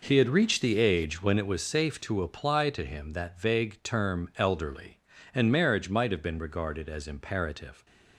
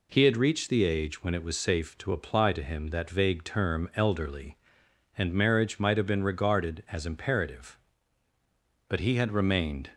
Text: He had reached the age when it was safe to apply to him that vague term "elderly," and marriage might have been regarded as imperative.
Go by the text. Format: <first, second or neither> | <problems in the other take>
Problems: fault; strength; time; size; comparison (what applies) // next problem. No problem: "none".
first | goes on to say "But he had remained"; noticeable; from 8.8 s on; 1.0 s long